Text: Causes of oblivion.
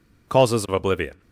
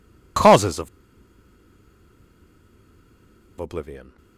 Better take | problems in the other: first | pauses between "of" and "oblivion"; strong; at 0.8 s; 2.7 s long

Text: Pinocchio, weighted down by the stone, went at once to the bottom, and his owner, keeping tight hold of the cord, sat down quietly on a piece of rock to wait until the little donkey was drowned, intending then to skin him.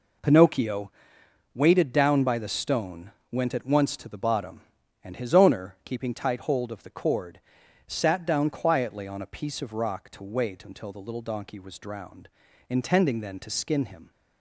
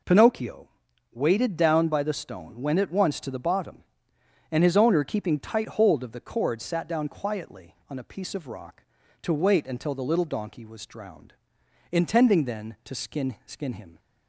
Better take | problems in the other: first | says "skin" twice; at 13.4 s

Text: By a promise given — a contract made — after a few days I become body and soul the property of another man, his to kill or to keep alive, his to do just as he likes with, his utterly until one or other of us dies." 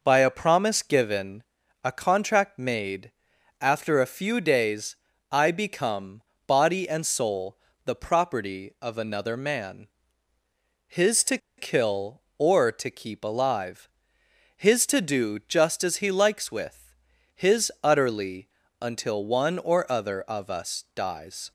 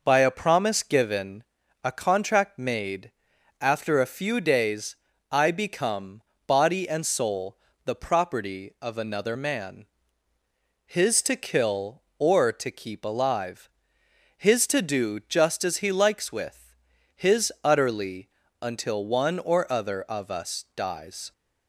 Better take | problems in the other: second | pauses between "days" and "I"; slight; at 4.9 s; 0.34 s long; slight in the second // pauses between "become" and "body"; slight; at 6.2 s; 0.26 s long; slight in the second // pauses between "soul" and "the"; slight; at 7.5 s; 0.28 s long; slight in the second // pauses between "to" and "kill"; slight; at 11.3 s; 0.20 s long // pauses between "utterly" and "until"; slight; at 18.4 s; 0.34 s long; slight in the second

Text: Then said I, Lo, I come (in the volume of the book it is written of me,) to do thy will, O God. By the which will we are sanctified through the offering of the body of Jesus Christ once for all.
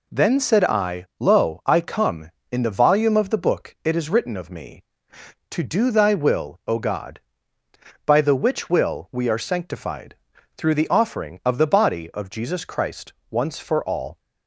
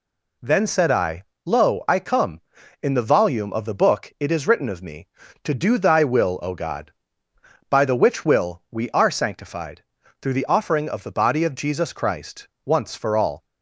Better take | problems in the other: neither | pauses between "sanctified" and "through"; the same in both // pauses between "Christ" and "once"; slight; the same in both

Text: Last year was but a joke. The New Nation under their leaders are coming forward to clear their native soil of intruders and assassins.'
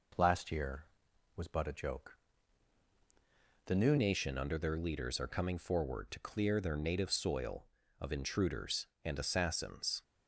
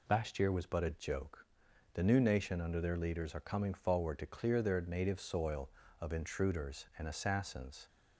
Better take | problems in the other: second | changes voice at "Nation"; from 3.9 s on; 6.1 s long

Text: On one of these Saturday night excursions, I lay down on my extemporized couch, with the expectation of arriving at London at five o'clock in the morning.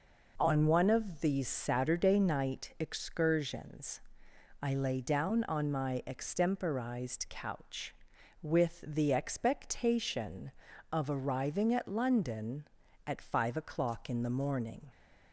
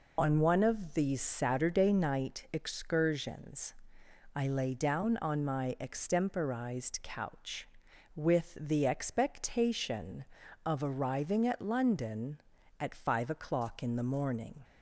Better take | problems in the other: first | loses the start of "On"; at 0.1 s; 95 ms

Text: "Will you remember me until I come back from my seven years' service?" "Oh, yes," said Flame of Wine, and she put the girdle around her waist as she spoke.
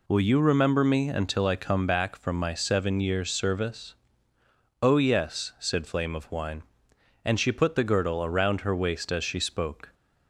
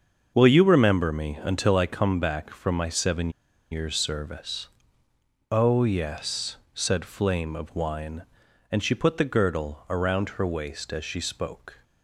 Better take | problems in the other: first | starts louder than the rest; until 1.3 s; 6.5 dB // pauses between "seven" and "years"; at 3.2 s; 0.41 s long

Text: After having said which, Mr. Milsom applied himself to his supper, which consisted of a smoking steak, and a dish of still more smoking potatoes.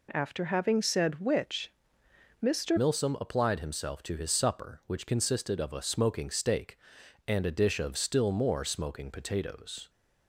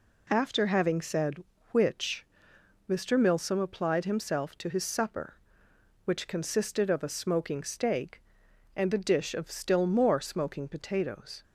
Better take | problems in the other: second | changes voice at "Milsom"; from 2.7 s on; 7.1 s long

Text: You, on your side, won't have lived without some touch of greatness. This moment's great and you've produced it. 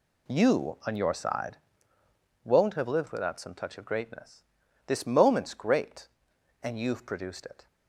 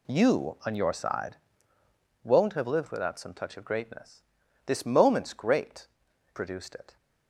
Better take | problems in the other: first | skips "and you've"; at 6.1 s

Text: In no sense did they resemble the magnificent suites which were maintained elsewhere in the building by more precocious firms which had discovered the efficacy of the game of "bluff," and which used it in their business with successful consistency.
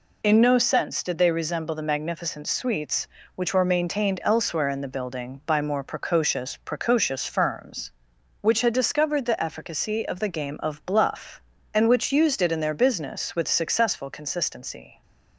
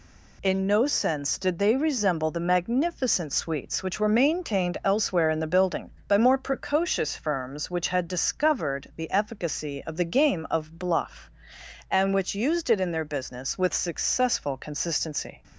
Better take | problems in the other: second | says "precocious" twice; at 6.6 s

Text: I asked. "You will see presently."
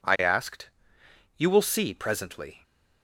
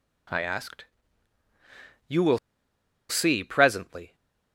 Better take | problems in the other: first | pauses between "will" and "see"; noticeable; at 2.3 s; 0.72 s long

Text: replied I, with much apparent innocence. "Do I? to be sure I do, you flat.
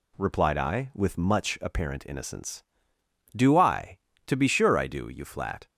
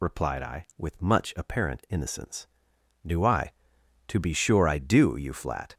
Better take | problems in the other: first | loses the start of "replied"; at 0.0 s; 40 ms

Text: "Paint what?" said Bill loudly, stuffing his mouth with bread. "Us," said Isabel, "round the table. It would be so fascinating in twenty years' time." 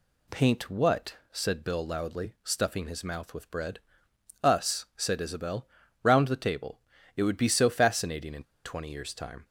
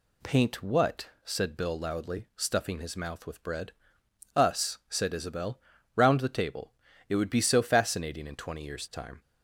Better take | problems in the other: second | pauses between "in" and "twenty"; slight; at 8.4 s; 0.21 s long

